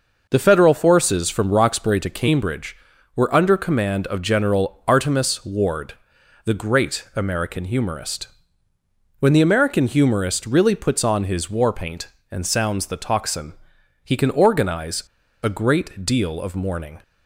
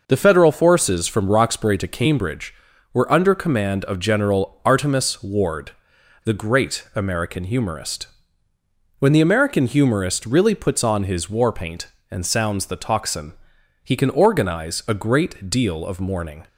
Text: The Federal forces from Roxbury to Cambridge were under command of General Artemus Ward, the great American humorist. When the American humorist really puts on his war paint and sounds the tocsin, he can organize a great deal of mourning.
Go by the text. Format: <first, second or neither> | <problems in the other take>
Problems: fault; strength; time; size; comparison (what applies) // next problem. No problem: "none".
second | pauses between "organize" and "a"; at 15.0 s; 0.41 s long